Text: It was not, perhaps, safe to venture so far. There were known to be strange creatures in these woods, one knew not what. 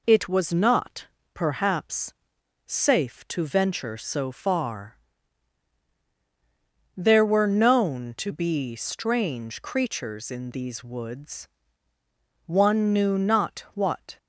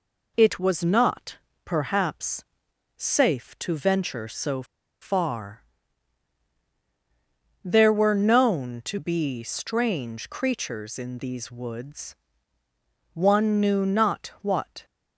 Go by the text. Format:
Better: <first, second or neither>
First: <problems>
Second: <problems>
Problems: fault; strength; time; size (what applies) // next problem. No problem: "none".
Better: first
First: none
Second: pauses between "so" and "far"; at 4.6 s; 0.37 s long